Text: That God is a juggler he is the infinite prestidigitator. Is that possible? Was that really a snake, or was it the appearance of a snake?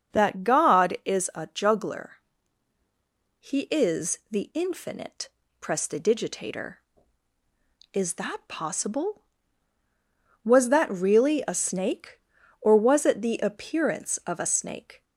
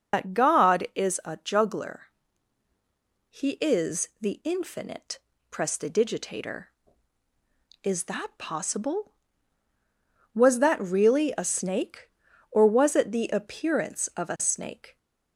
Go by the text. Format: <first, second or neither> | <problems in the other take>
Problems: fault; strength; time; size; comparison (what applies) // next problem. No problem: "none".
first | loses the start of "That"; at 0.1 s; 110 ms // pauses between "juggler" and "he"; strong; at 2.0 s; 1.3 s long; strong in the first // pauses between "infinite" and "prestidigitator"; slight; at 5.2 s; 0.32 s long; slight in the first